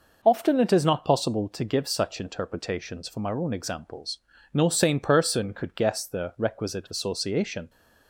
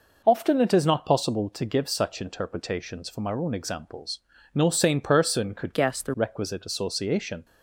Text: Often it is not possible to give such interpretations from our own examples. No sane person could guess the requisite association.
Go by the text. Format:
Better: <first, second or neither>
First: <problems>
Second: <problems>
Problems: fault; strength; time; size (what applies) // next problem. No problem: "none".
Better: first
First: none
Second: changes voice from "guess" to "the"; from 5.7 to 6.1 s; 0.4 s long